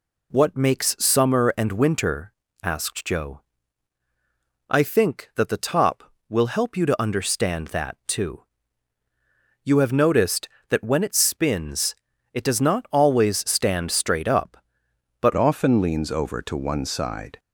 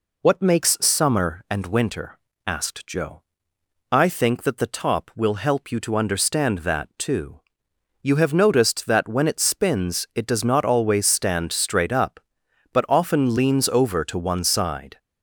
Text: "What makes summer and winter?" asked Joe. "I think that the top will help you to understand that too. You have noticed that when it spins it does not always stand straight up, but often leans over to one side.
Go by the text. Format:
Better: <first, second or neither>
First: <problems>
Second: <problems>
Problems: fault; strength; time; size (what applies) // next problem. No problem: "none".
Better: second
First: pauses between "spins" and "it"; at 11.9 s; 0.38 s long // changes voice at "often"; from 15.3 s on; 2.0 s long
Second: none